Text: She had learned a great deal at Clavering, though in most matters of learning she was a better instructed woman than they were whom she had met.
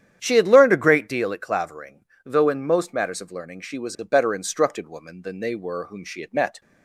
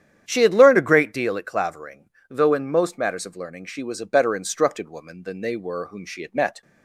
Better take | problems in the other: neither | starts louder than the rest; strong; the same in both

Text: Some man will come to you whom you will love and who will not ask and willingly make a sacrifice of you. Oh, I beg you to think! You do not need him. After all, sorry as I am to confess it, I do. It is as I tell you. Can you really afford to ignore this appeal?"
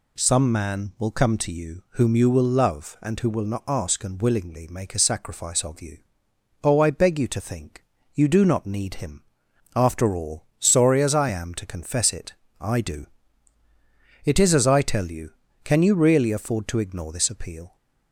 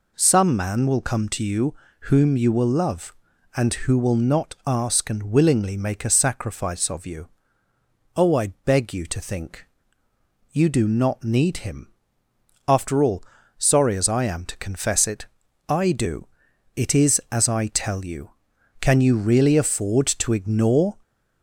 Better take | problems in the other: first | pauses between "you" and "whom"; slight; at 1.7 s; 0.28 s long // pauses between "I" and "beg"; slight; at 8.4 s; 0.18 s long // stops before "this appeal"; at 21.0 s

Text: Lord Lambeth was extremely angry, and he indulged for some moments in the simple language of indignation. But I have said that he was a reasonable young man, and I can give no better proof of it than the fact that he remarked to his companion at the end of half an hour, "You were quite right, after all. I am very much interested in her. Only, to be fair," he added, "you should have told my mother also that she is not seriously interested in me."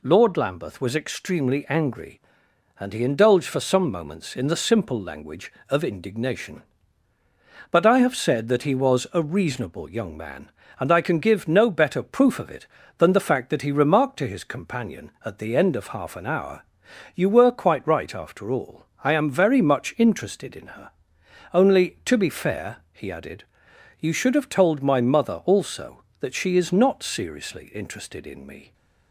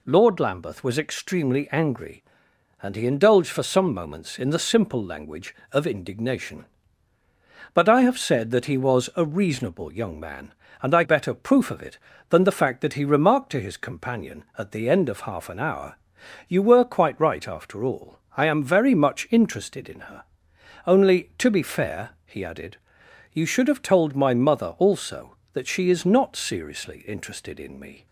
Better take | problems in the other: first | skips "can give no"; at 11.0 s

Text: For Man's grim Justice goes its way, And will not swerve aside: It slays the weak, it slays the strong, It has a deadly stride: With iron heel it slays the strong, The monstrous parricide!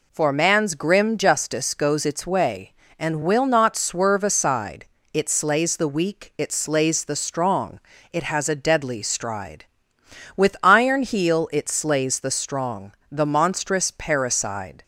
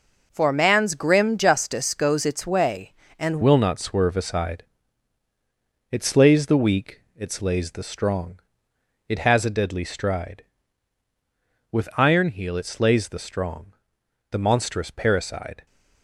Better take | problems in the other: first | changes voice at "will"; from 3.4 s on; 12.2 s long

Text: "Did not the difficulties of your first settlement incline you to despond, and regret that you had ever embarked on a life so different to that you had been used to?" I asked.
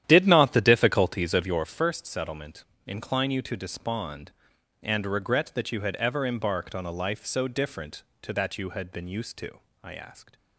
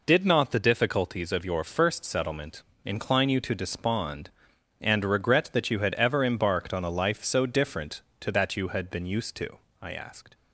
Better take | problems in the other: second | starts louder than the rest; strong; until 1.8 s; 11 dB // pauses between "settlement" and "incline"; slight; at 2.6 s; 0.22 s long; slight in the second

